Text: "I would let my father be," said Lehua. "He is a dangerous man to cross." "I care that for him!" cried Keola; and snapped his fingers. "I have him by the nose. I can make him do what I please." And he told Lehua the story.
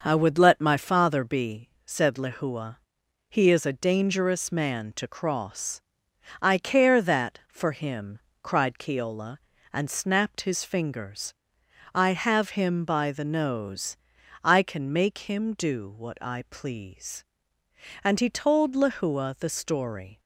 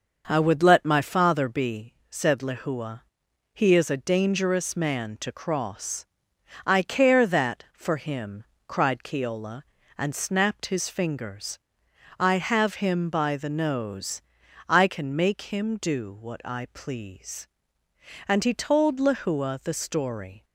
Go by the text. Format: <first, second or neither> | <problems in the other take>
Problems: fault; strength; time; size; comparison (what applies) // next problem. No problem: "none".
neither | starts louder than the rest; noticeable; the same in both